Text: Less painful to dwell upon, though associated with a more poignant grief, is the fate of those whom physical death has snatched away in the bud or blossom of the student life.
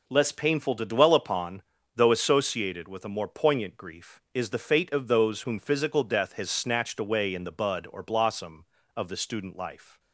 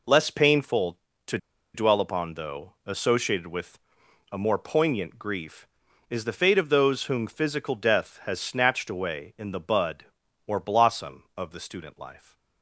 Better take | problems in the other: first | pauses between "to" and "dwell"; at 1.3 s; 0.36 s long // pauses between "with" and "a"; noticeable; at 3.7 s; 0.52 s long

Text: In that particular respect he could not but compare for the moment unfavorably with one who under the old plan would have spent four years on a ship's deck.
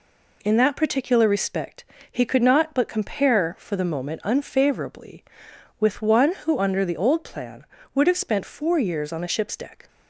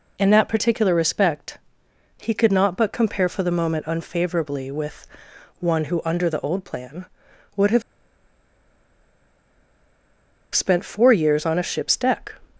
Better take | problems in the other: first | pauses between "respect" and "he"; noticeable; at 1.5 s; 0.64 s long; slight in the first // pauses between "with" and "one"; noticeable; at 5.0 s; 0.52 s long // pauses between "have" and "spent"; strong; at 7.8 s; 2.7 s long

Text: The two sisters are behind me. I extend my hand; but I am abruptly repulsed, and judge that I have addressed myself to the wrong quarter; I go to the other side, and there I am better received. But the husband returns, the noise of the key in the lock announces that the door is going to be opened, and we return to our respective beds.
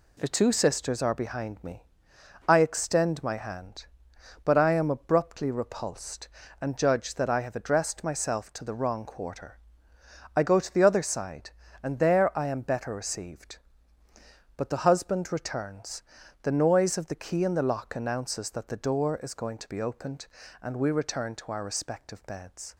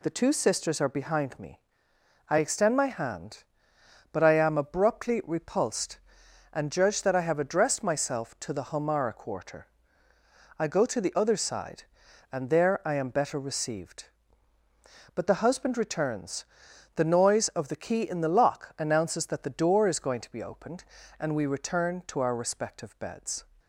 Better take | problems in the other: first | says "homara" for "wrong"; at 8.7 s

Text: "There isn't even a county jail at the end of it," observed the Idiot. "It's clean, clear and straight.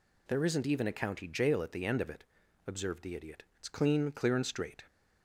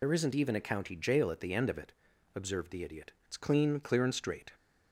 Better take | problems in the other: first | loses the start of "There"; at 0.0 s; 60 ms

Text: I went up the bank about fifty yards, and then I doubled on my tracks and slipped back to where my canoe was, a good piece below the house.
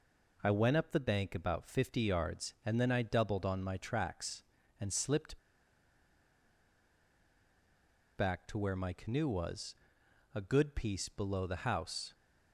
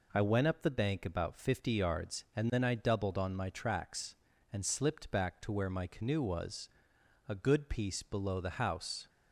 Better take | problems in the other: second | pauses between "slipped" and "back"; strong; at 5.3 s; 2.8 s long

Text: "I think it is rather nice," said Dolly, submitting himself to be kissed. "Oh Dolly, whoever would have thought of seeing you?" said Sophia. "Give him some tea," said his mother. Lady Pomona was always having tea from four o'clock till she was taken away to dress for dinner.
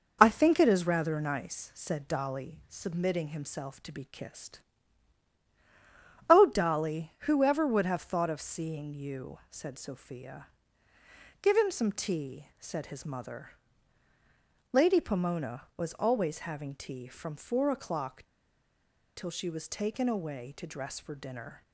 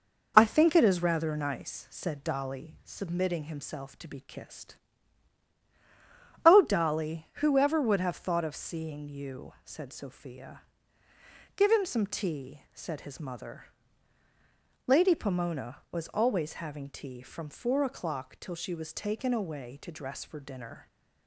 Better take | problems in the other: second | pauses between "o'clock" and "till"; noticeable; at 18.2 s; 0.90 s long

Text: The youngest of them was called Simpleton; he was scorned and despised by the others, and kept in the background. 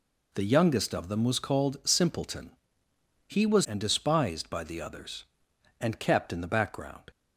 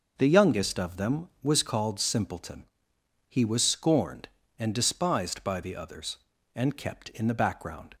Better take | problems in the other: second | skips "scorned"; at 3.6 s

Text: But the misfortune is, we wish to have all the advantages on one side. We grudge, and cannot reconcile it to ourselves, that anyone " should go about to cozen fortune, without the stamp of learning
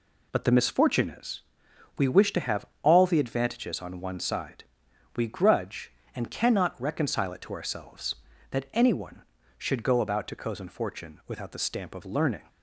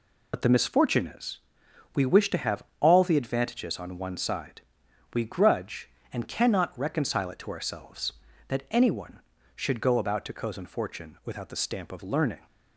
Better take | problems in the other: first | loses the start of "But"; at 0.3 s; 40 ms // pauses between "have" and "all"; slight; at 2.6 s; 0.16 s long; slight in the first

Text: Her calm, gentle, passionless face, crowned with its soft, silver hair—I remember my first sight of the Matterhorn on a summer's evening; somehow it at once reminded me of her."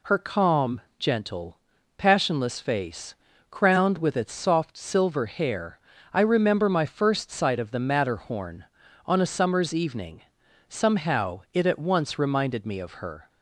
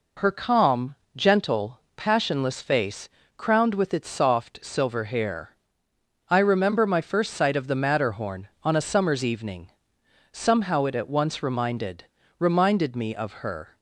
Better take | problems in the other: first | says "reminded" twice; at 12.3 s

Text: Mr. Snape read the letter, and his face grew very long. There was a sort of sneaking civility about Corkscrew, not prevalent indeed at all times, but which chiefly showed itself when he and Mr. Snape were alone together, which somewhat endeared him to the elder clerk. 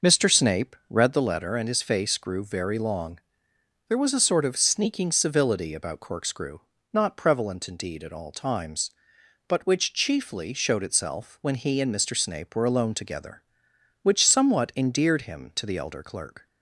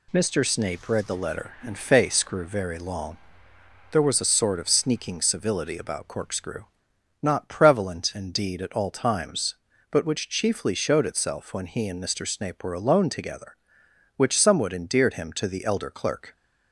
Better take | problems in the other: first | skips "his"; at 1.7 s

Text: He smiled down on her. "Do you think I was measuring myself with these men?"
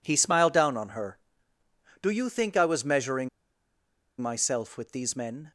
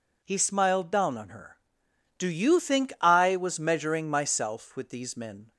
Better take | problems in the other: second | pauses between "measuring" and "myself"; noticeable; at 3.2 s; 0.92 s long

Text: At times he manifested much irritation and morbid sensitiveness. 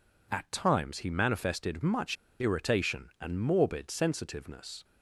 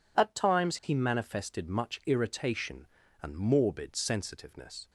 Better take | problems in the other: second | pauses between "much" and "irritation"; slight; at 2.1 s; 0.24 s long

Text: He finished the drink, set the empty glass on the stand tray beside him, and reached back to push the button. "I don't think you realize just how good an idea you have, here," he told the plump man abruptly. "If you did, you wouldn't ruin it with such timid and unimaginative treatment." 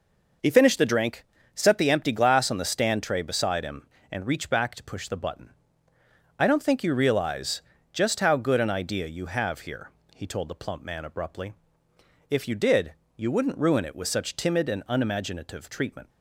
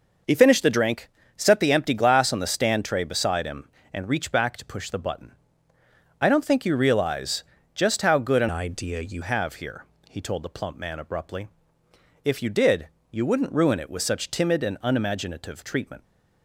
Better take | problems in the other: first | pauses between "realize" and "just"; slight; at 7.4 s; 0.32 s long; slight in the first // changes voice from "idea" to "you"; from 8.4 to 9.2 s; 0.8 s long

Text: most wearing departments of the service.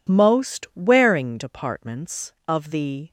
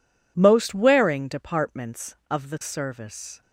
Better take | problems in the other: second | stops before "service"; at 3.0 s

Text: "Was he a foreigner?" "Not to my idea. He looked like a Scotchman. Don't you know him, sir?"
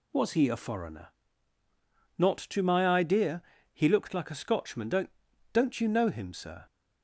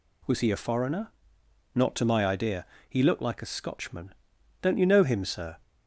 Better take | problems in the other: second | says "Don't" twice; at 5.5 s

